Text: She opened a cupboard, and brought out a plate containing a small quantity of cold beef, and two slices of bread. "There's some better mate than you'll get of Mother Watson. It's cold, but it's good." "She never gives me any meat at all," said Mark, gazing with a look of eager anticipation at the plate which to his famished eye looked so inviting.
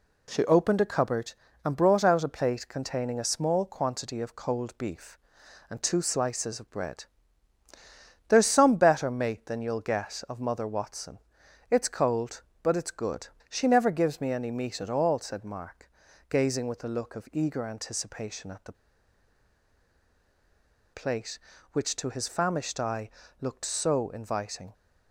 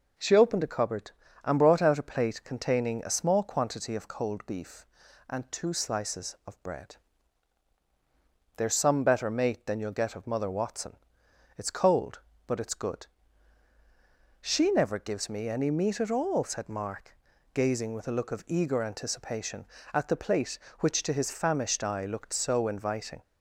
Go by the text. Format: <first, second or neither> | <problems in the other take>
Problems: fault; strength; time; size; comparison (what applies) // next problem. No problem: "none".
second | pauses between "the" and "plate"; strong; at 18.7 s; 2.2 s long // pauses between "eye" and "looked"; slight; at 23.0 s; 0.32 s long